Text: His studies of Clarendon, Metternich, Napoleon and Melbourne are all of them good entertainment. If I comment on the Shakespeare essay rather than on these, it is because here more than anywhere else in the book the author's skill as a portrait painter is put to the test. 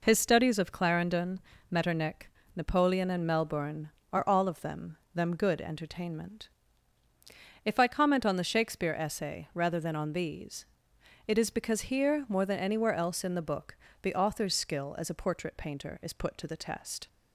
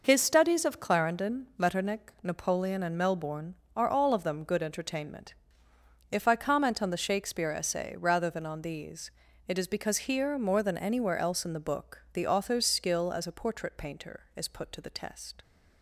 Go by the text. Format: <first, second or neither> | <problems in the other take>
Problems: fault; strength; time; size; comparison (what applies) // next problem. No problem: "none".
second | says "them" twice; at 5.1 s // pauses between "book" and "the"; slight; at 13.7 s; 0.24 s long